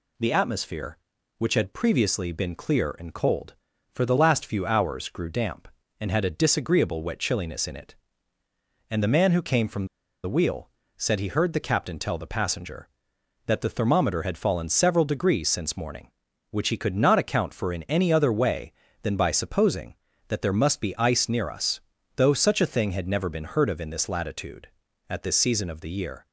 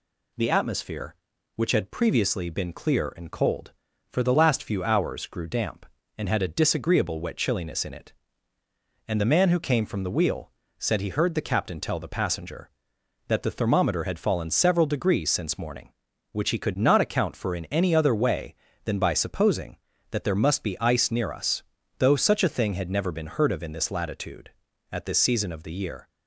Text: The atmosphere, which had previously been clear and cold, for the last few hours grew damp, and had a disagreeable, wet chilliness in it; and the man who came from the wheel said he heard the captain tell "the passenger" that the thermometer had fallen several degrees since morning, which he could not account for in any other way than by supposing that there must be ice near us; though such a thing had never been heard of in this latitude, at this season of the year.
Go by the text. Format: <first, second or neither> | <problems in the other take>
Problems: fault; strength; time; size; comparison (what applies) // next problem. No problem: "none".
second | pauses between "from" and "the"; at 9.8 s; 0.38 s long // pauses between "wheel" and "said"; slight; at 10.6 s; 0.28 s long; slight in the second